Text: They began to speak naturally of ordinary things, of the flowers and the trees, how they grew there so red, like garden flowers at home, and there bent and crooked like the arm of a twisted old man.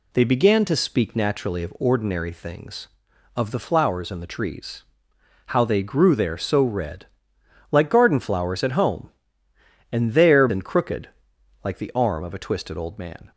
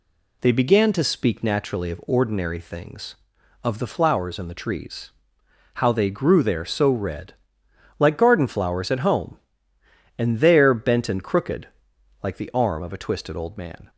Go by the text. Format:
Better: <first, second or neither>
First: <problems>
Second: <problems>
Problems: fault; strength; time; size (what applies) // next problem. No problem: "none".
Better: second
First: skips "bent"; at 10.4 s // pauses between "crooked" and "like"; noticeable; at 11.0 s; 0.54 s long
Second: pauses between "crooked" and "like"; noticeable; at 11.6 s; 0.54 s long